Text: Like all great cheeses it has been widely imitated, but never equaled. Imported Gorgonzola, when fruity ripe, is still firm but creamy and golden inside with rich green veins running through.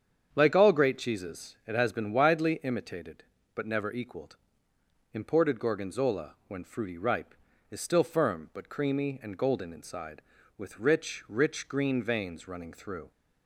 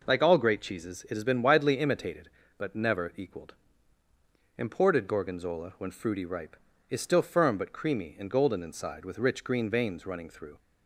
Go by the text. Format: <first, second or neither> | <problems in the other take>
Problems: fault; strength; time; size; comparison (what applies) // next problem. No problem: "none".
second | starts louder than the rest; strong; until 1.3 s; 8 dB // says "rich" twice; at 11.2 s